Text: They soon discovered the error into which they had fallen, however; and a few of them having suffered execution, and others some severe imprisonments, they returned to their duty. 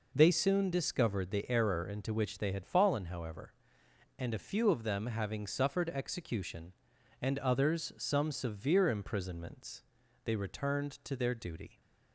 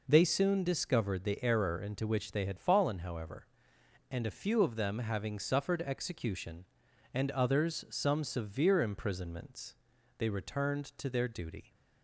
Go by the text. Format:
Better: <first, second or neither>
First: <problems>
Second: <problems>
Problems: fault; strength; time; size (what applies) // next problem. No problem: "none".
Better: neither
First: none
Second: none